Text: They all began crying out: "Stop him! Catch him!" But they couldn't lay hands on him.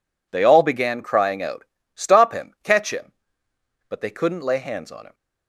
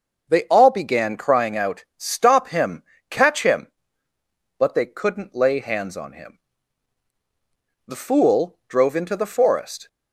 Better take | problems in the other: first | starts louder than the rest; until 1.3 s; 6.5 dB // goes on to say "The fool drove into the forest"; strong; from 7.8 s on; 2.0 s long

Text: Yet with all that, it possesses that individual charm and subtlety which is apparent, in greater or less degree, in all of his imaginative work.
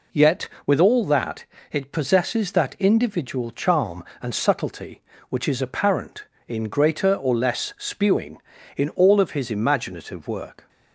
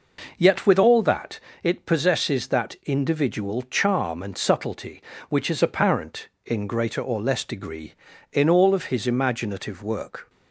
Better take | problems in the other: second | says "spewing" for "degree"; at 7.7 s

